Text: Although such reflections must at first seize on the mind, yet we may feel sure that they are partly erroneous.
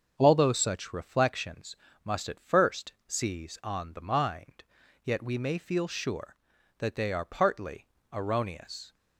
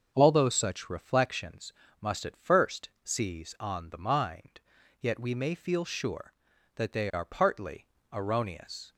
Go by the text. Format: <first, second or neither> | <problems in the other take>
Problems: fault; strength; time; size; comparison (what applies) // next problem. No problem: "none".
neither | starts louder than the rest; the same in both // pauses between "reflections" and "must"; slight; the same in both // pauses between "partly" and "erroneous"; slight; the same in both